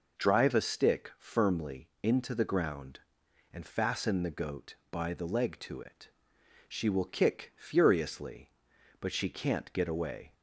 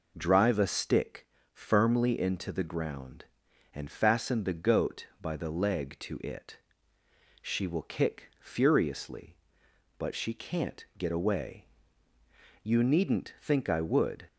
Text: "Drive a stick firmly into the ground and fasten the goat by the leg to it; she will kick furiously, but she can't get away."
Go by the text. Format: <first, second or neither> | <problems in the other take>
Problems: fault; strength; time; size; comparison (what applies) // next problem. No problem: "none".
first | pauses between "stick" and "firmly"; slight; at 1.2 s; 0.28 s long // goes on to say "You needn't think I would"; from 12.6 s on; 1.6 s long